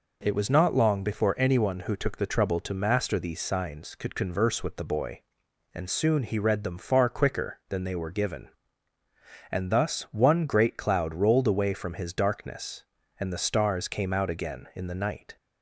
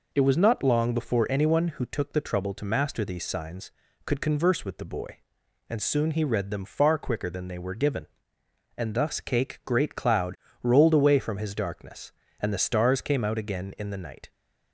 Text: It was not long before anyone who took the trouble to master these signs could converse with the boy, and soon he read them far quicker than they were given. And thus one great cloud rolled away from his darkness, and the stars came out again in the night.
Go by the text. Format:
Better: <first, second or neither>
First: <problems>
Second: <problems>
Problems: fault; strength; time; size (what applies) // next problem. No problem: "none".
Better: first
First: none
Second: says "cake" for "one"; at 9.1 s // pauses between "cloud" and "rolled"; slight; at 10.3 s; 0.26 s long